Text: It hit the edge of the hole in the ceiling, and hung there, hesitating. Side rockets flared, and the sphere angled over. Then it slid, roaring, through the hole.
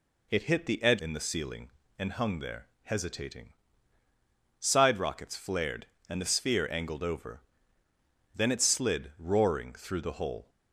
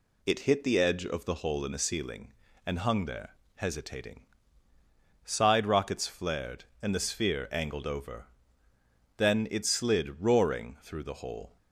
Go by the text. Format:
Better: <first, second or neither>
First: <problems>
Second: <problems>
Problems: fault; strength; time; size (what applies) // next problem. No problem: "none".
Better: second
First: skips "of the hole"; at 1.0 s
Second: none